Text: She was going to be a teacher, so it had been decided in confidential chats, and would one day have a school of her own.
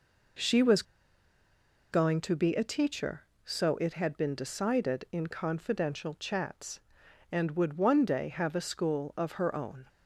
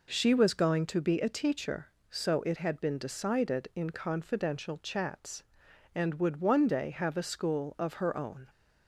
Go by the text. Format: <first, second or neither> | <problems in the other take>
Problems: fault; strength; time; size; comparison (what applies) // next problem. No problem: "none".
second | pauses between "was" and "going"; at 0.8 s; 1.0 s long